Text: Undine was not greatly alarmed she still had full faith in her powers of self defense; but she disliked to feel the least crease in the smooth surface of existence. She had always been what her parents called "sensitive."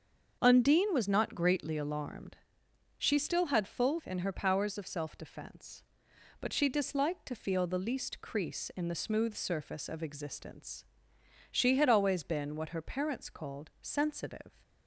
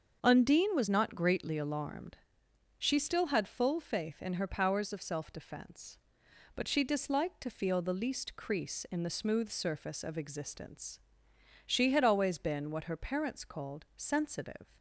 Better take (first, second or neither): second